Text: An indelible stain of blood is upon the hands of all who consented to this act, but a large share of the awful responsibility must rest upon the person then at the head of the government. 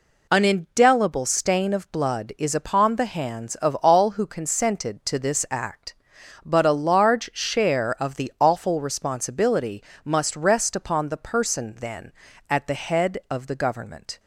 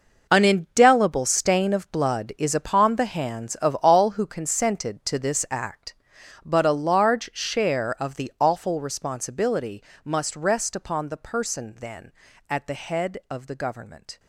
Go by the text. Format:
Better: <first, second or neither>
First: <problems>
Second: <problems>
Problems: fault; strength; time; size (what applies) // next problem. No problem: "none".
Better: first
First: pauses between "responsibility" and "must"; slight; at 9.8 s; 0.22 s long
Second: gets quieter; strong; throughout; 12 dB // pauses between "responsibility" and "must"; slight; at 9.8 s; 0.22 s long